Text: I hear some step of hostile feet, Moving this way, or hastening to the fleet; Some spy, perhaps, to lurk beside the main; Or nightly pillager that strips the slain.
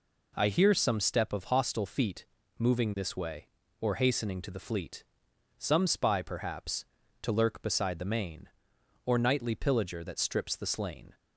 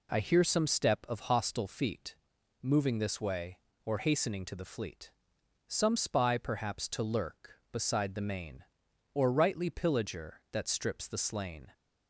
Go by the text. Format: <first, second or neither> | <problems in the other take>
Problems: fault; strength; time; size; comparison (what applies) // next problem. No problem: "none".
first | says "rightly" for "nightly"; at 9.3 s